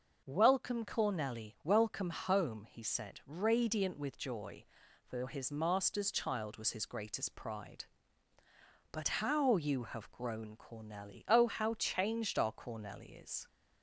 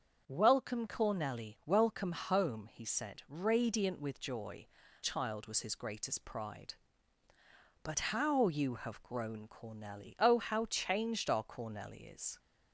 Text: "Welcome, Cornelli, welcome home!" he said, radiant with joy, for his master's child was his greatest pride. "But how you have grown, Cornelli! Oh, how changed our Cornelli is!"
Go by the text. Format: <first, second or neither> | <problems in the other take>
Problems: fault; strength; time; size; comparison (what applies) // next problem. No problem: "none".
first | starts louder than the rest; strong; until 1.2 s; 7 dB; also in the first // skips "for his master's"; at 4.8 s